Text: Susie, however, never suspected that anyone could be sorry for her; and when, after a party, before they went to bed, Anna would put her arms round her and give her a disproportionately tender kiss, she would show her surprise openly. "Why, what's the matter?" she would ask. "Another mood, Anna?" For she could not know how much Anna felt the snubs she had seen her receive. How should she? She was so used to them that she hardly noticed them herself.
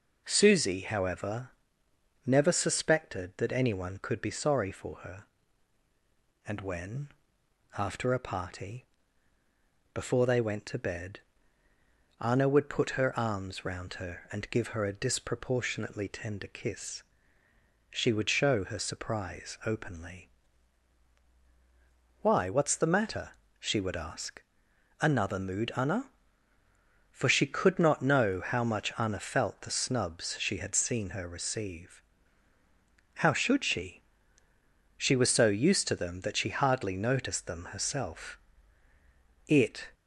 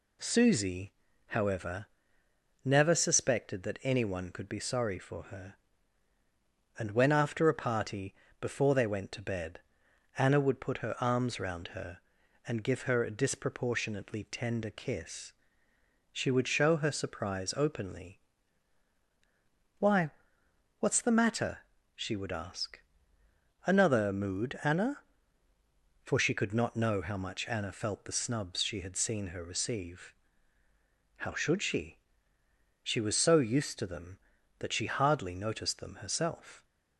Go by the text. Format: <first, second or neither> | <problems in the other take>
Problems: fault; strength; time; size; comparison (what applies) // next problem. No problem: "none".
second | goes on to say "It"; slight; from 39.4 s on; 0.48 s long